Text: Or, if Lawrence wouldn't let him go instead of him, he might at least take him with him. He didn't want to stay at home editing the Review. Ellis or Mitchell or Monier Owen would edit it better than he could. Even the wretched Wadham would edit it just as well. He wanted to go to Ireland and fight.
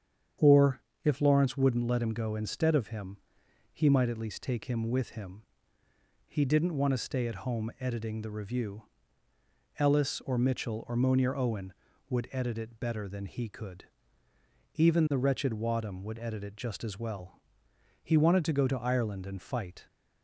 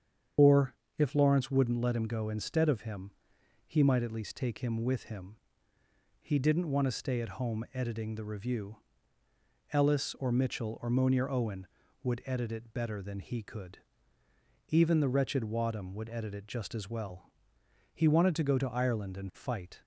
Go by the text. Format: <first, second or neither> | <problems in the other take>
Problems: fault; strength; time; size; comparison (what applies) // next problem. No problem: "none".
first | loses the start of "Or"; at 0.3 s; 55 ms // starts louder than the rest; strong; until 1.6 s; 8 dB; strong in the first